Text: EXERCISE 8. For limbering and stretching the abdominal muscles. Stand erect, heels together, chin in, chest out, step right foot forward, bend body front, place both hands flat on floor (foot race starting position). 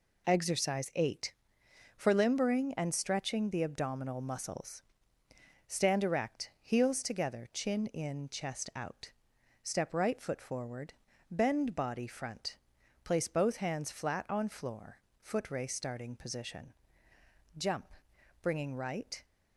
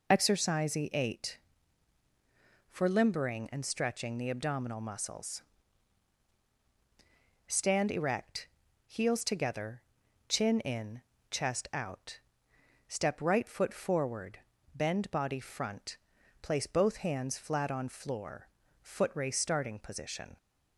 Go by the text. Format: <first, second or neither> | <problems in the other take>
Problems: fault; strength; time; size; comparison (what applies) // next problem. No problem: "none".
second | goes on to say "Jump bringing right"; strong; from 17.5 s on; 1.7 s long